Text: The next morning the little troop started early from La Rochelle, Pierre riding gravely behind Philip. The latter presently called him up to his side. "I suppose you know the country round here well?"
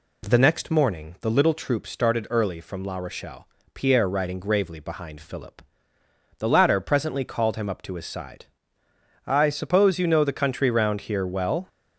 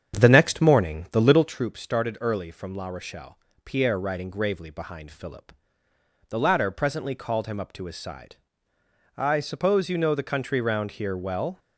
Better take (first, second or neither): first